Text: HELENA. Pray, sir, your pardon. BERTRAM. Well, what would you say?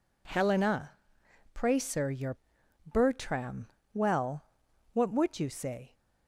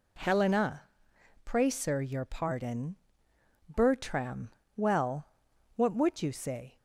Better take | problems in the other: second | skips "pardon"; at 2.6 s

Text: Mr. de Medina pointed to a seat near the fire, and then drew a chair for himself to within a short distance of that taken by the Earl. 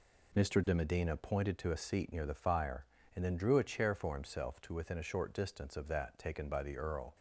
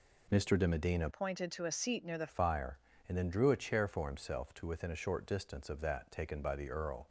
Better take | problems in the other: first | changes voice from "pointed" to "the"; from 1.1 to 2.2 s; 1.1 s long

